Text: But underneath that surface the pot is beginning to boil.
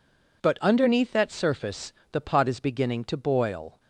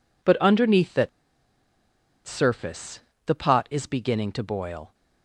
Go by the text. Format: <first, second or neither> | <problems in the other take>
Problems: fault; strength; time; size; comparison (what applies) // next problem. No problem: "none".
first | pauses between "that" and "surface"; at 1.0 s; 1.1 s long // pauses between "surface" and "the"; slight; at 2.9 s; 0.26 s long; slight in the first